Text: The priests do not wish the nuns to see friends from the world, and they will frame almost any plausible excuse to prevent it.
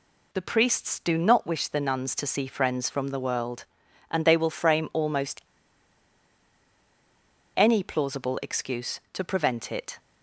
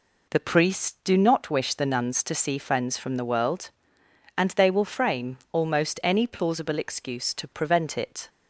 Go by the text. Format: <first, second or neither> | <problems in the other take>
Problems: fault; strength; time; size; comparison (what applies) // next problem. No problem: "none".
second | pauses between "almost" and "any"; strong; at 5.4 s; 2.1 s long